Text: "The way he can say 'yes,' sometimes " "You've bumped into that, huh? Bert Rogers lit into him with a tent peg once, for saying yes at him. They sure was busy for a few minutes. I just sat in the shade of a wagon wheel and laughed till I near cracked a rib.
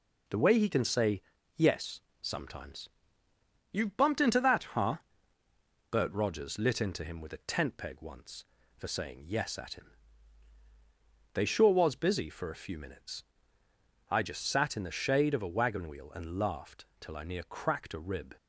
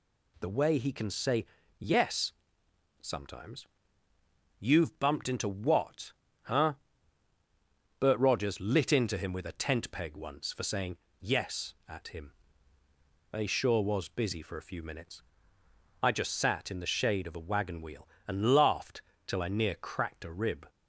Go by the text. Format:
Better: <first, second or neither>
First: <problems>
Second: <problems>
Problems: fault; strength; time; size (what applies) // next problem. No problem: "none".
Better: first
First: pauses between "say" and "yes"; slight; at 1.2 s; 0.34 s long // pauses between "laughed" and "till"; slight; at 16.8 s; 0.16 s long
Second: pauses between "say" and "yes"; slight; at 1.4 s; 0.34 s long // says "what" for "that"; at 5.4 s // pauses between "saying" and "yes"; slight; at 10.9 s; 0.24 s long // pauses between "laughed" and "till"; slight; at 19.0 s; 0.26 s long